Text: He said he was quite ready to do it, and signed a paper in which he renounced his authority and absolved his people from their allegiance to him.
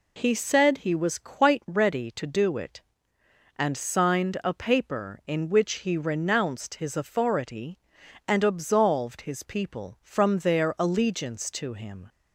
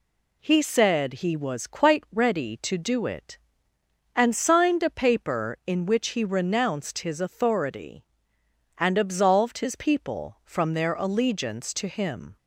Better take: neither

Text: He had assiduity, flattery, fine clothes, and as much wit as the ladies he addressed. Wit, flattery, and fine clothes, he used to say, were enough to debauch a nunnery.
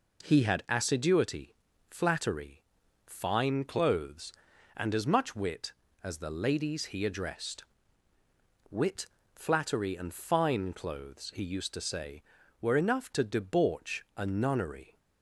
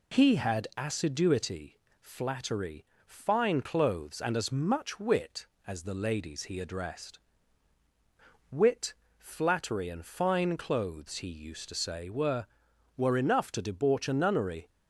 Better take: first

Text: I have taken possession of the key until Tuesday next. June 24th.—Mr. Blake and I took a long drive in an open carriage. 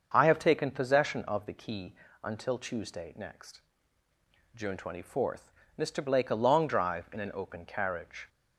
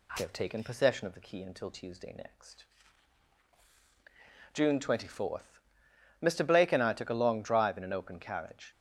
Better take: second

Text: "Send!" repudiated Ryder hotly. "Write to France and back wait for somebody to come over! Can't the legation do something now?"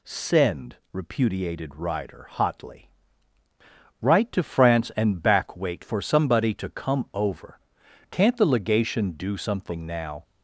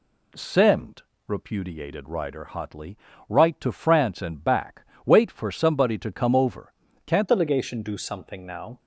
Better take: first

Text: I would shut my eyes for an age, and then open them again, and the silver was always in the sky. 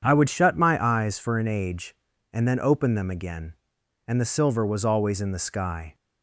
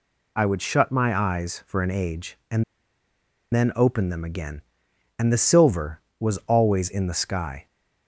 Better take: first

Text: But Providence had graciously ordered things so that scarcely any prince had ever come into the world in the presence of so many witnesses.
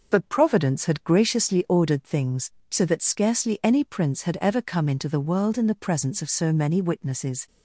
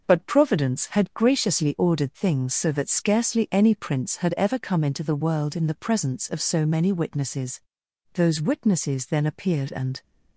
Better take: first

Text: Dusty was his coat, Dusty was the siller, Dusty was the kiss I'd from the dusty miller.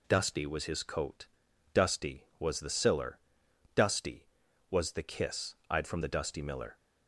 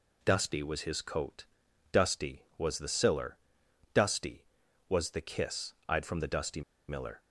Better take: first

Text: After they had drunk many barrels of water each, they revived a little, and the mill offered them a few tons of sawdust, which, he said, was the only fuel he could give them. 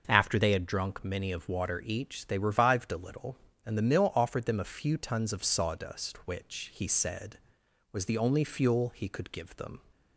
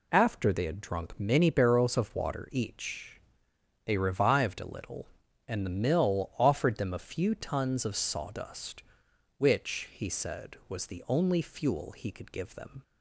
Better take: second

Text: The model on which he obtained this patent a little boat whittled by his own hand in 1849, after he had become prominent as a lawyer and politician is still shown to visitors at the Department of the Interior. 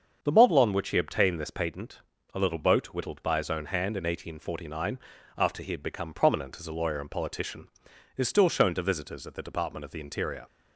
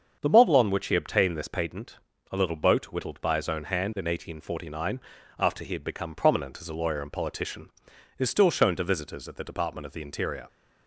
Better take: neither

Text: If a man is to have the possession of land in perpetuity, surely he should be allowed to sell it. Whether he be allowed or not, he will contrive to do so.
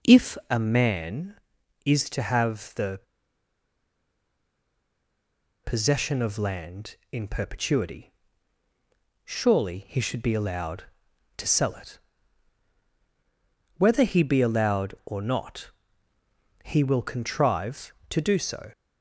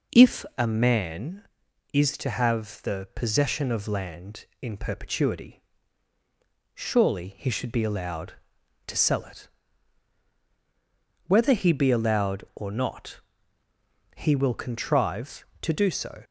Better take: second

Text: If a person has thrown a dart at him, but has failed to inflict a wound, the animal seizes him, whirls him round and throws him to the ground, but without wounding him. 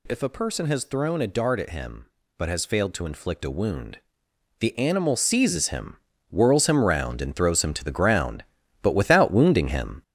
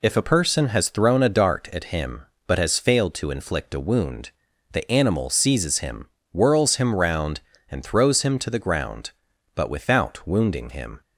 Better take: second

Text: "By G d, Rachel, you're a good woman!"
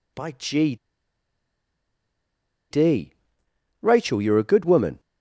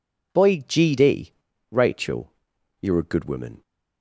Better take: second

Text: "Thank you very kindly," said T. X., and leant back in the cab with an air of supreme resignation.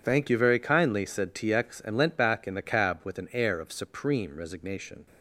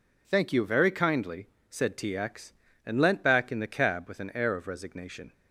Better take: first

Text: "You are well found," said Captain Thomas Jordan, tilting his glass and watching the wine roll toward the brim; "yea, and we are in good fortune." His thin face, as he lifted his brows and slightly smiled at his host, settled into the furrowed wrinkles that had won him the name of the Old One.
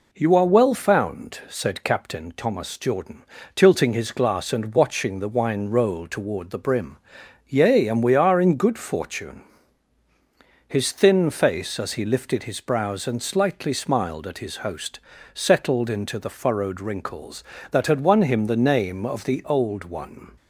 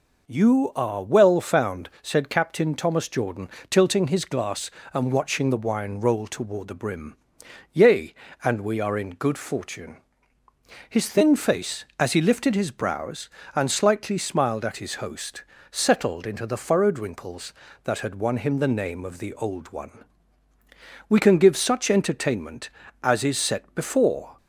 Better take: first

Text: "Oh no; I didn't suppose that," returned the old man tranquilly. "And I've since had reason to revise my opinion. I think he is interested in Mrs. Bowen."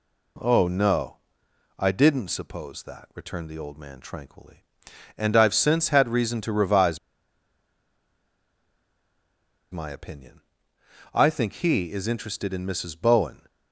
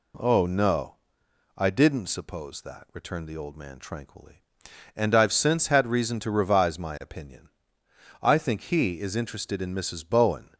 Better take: second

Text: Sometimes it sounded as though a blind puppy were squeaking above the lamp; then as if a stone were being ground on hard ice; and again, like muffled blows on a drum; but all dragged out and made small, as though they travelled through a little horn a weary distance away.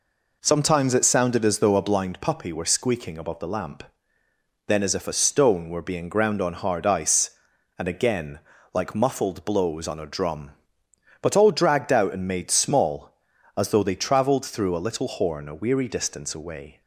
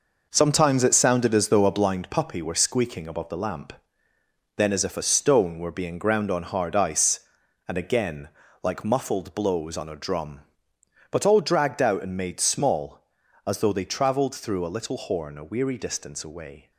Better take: first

